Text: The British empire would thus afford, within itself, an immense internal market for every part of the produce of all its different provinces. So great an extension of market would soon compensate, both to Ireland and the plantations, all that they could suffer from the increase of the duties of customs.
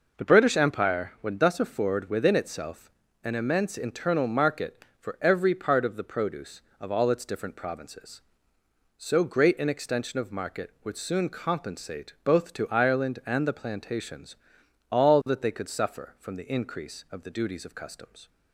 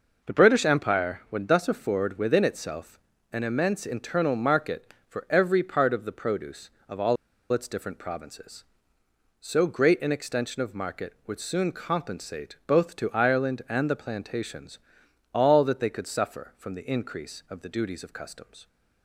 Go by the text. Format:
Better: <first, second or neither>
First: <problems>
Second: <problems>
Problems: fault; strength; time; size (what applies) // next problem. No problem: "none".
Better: first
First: none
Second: pauses between "all" and "its"; at 7.1 s; 0.37 s long